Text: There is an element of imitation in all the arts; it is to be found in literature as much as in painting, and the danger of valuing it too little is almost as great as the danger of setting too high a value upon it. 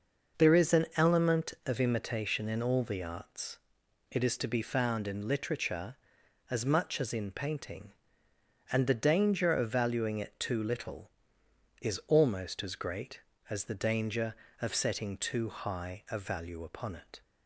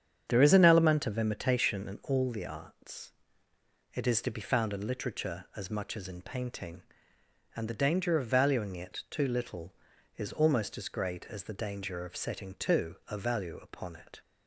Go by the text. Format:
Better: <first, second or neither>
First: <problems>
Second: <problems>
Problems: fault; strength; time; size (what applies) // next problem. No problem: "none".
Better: first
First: none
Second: starts louder than the rest; strong; until 1.2 s; 8 dB // skips "high"; at 13.0 s